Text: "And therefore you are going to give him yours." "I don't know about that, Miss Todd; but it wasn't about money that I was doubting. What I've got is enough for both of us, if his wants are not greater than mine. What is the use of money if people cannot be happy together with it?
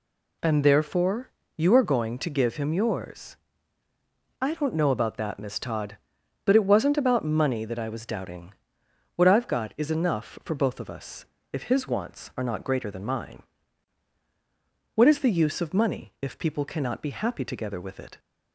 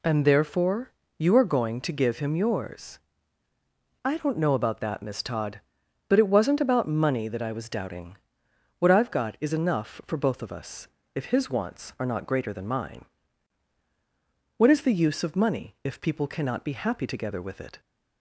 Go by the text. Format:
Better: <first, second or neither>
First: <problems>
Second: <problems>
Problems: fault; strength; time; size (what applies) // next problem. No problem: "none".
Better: neither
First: pauses between "therefore" and "you"; slight; at 1.3 s; 0.26 s long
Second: pauses between "therefore" and "you"; slight; at 0.9 s; 0.26 s long